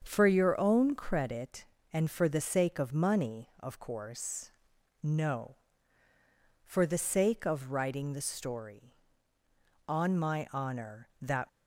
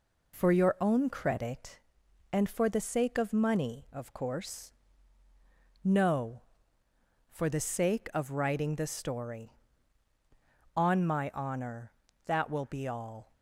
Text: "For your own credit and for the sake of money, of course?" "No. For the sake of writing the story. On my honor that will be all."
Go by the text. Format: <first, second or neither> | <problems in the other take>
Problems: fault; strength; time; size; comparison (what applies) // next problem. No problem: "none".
second | starts louder than the rest; until 1.0 s; 7 dB // stops before "will be all"; at 11.4 s